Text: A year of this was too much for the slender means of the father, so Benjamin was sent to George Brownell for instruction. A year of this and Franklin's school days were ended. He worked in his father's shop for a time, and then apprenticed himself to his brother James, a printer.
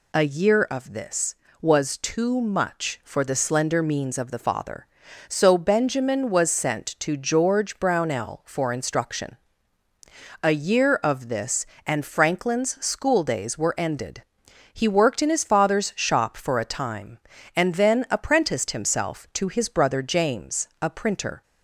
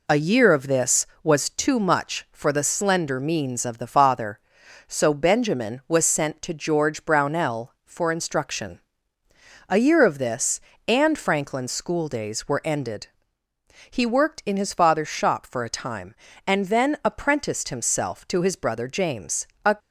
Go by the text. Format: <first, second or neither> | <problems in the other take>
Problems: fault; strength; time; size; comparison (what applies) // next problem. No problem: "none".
first | stops before "printer"; at 19.7 s